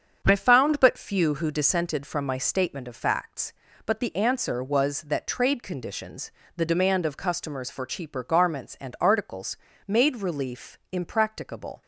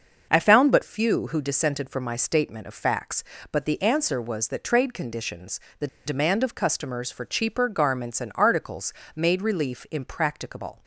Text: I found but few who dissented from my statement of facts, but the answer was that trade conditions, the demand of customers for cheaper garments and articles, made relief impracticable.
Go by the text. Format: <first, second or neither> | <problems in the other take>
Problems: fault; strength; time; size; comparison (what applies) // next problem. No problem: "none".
first | starts louder than the rest; until 1.3 s; 6.5 dB; strong in the first // pauses between "the" and "demand"; slight; at 5.8 s; 0.19 s long